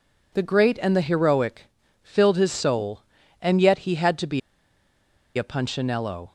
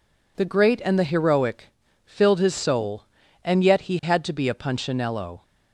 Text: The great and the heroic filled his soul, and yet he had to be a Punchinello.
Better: second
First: pauses between "heroic" and "filled"; slight; at 1.7 s; 0.32 s long // pauses between "be" and "a"; noticeable; at 4.3 s; 0.97 s long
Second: pauses between "heroic" and "filled"; slight; at 1.7 s; 0.32 s long

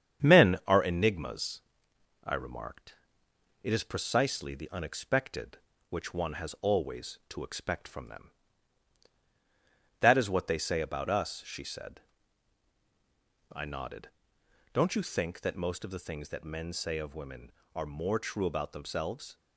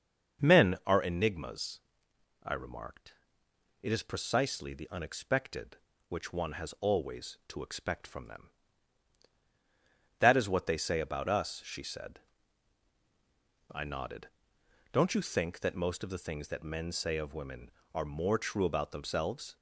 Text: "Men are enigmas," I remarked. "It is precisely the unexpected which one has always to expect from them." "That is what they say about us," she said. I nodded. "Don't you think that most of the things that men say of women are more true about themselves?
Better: second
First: gets quieter; throughout; 3.5 dB // starts louder than the rest; strong; until 1.3 s; 8.5 dB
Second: starts louder than the rest; until 1.4 s; 6.5 dB

